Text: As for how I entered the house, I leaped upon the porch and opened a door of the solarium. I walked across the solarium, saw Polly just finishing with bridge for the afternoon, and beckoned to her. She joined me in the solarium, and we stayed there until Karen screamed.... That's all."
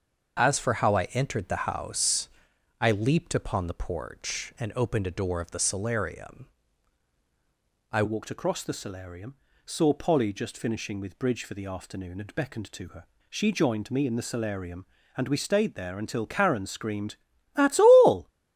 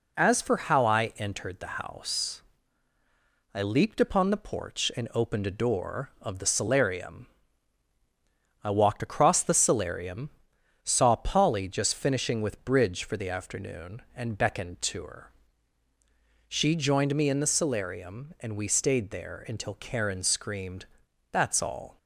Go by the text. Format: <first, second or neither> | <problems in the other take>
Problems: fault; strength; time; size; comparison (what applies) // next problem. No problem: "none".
second | starts louder than the rest; until 1.4 s; 6.5 dB // changes voice at "walked"; from 8.0 s on; 10.2 s long